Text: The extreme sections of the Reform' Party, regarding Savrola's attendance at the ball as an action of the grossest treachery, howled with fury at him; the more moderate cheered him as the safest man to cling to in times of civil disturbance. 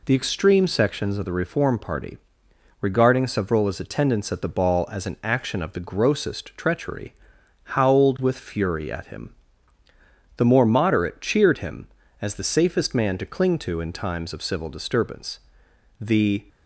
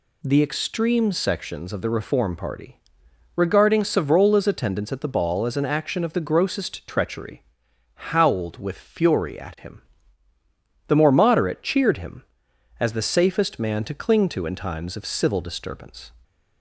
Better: second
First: goes on to say "The"; slight; from 15.9 s on; 0.44 s long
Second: none

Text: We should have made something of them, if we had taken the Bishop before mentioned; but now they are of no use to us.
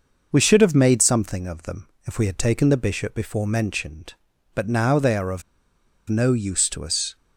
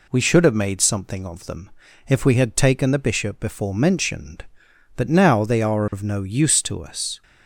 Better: second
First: pauses between "of" and "no"; noticeable; at 5.4 s; 0.67 s long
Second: none

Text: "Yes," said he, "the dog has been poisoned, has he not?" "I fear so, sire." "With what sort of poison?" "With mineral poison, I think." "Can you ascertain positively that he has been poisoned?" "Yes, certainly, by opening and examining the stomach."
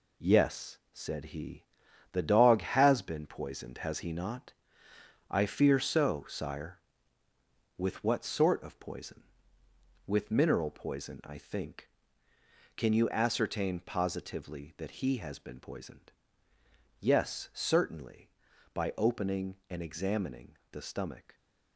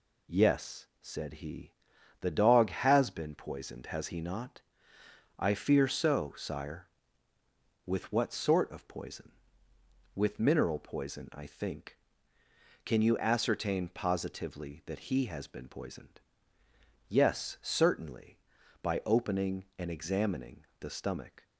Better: second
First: gets quieter; throughout; 7 dB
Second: none

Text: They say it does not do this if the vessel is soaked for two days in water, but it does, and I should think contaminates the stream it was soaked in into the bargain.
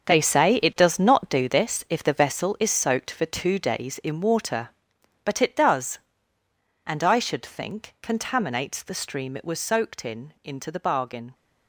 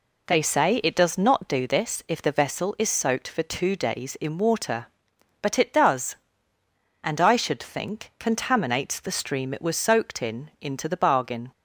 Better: second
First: gets quieter; strong; throughout; 12 dB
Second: none

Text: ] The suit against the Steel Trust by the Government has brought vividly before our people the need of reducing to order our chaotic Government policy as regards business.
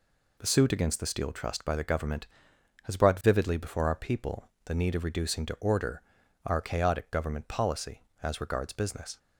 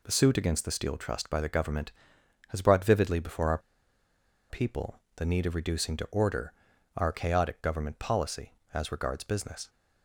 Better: first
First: pauses between "people" and "the"; slight; at 4.4 s; 0.16 s long // pauses between "order" and "our"; at 6.0 s; 0.44 s long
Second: pauses between "our" and "people"; noticeable; at 3.5 s; 0.91 s long // pauses between "people" and "the"; slight; at 4.9 s; 0.16 s long // pauses between "order" and "our"; at 6.5 s; 0.44 s long

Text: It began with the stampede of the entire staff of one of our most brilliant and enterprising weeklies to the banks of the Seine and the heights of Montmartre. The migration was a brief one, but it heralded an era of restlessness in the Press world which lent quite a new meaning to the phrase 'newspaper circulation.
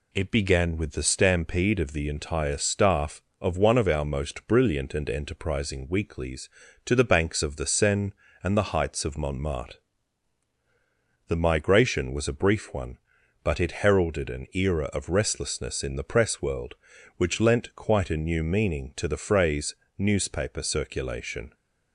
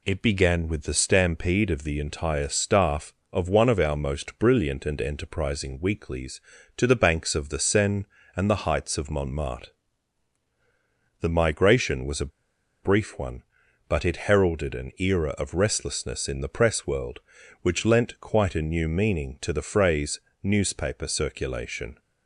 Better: first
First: pauses between "phrase" and "newspaper"; slight; at 19.7 s; 0.24 s long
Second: pauses between "a" and "brief"; noticeable; at 12.3 s; 0.53 s long // pauses between "phrase" and "newspaper"; slight; at 20.2 s; 0.24 s long

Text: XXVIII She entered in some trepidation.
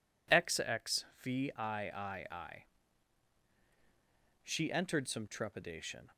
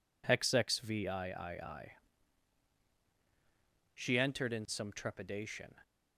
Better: second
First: pauses between "XXVIII" and "She"; strong; at 1.5 s; 2.9 s long // skips "in"; at 5.0 s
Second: pauses between "XXVIII" and "She"; strong; at 1.3 s; 2.5 s long

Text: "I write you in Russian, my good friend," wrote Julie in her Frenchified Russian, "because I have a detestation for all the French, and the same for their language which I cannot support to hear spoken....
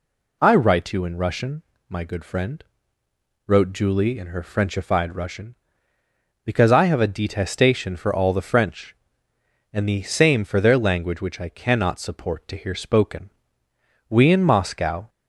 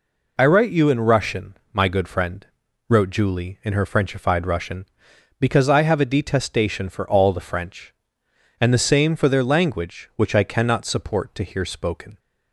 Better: second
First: goes on to say "We in Moscow"; noticeable; from 14.0 s on; 1.0 s long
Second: none

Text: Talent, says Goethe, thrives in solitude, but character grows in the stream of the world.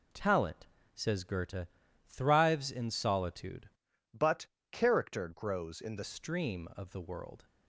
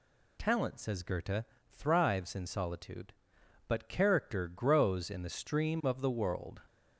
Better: second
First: changes voice from "but" to "the"; from 4.1 to 6.0 s; 1.9 s long // pauses between "but" and "character"; slight; at 4.4 s; 0.22 s long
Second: none

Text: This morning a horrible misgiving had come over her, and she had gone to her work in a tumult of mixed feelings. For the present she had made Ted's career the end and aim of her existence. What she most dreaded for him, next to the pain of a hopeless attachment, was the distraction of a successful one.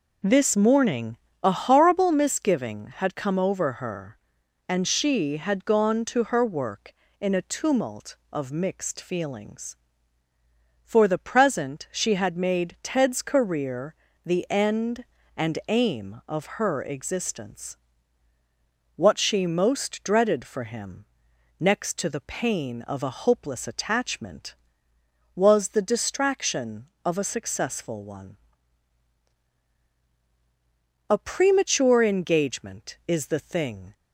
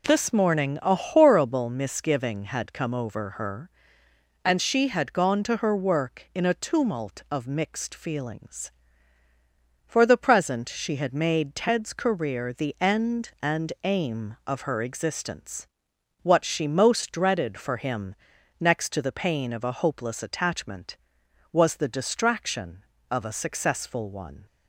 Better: second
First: pauses between "morning" and "a"; slight; at 1.1 s; 0.26 s long // pauses between "career" and "the"; slight; at 13.9 s; 0.30 s long // goes on to say "A premature engagement is the thing"; strong; from 31.0 s on; 2.8 s long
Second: none

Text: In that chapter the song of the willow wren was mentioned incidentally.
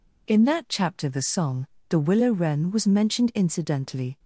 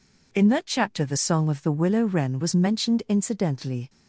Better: second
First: skips "of"; at 1.7 s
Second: none

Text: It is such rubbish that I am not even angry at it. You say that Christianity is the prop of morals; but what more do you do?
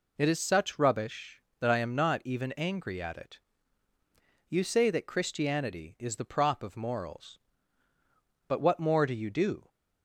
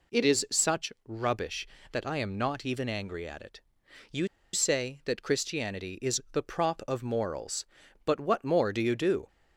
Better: first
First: none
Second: pauses between "You" and "say"; slight; at 4.2 s; 0.25 s long

